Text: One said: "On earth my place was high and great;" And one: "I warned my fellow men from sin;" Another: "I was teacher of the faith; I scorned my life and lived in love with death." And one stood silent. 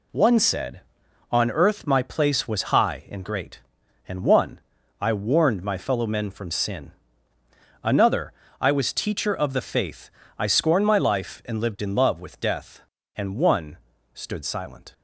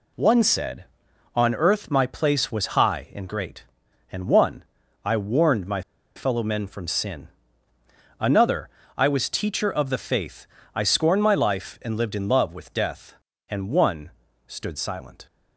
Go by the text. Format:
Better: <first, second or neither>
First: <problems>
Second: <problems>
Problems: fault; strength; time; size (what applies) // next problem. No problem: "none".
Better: first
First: pauses between "one" and "stood"; slight; at 13.7 s; 0.34 s long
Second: pauses between "my" and "fellow"; slight; at 5.8 s; 0.34 s long // pauses between "one" and "stood"; slight; at 14.1 s; 0.34 s long